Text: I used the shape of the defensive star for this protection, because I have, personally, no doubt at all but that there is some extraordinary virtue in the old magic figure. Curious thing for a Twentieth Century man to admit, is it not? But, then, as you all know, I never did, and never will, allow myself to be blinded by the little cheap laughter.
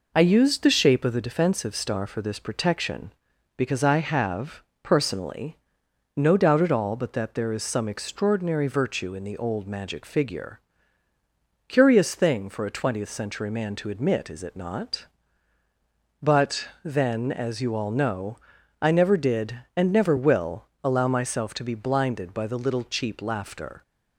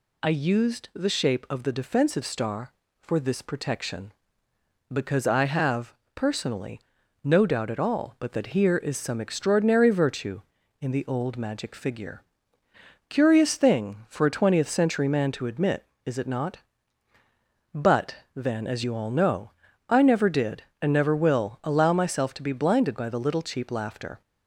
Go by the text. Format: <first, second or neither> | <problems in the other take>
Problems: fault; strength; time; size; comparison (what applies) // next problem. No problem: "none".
first | says "here" for "there"; at 8.4 s